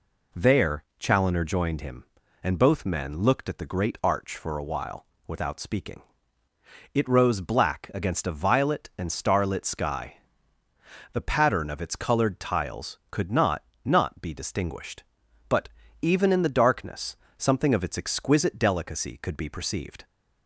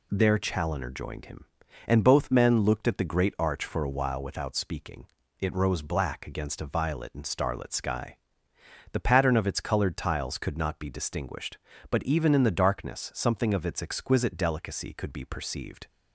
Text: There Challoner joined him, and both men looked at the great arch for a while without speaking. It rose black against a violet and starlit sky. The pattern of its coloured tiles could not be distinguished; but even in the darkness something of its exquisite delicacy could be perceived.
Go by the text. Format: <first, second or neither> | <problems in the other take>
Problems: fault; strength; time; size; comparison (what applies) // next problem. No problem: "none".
second | pauses between "while" and "without"; slight; at 5.0 s; 0.20 s long // says "not" twice; at 13.8 s // pauses between "but" and "even"; slight; at 15.6 s; 0.32 s long // pauses between "darkness" and "something"; slight; at 17.1 s; 0.20 s long